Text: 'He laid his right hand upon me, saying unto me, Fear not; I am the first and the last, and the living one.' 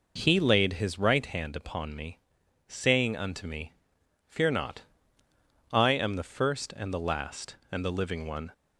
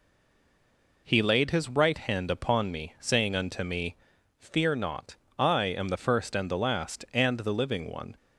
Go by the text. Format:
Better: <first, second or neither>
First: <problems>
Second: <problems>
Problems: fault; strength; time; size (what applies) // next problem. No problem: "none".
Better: first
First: none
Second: stays silent before the first word; until 1.0 s; 1.0 s long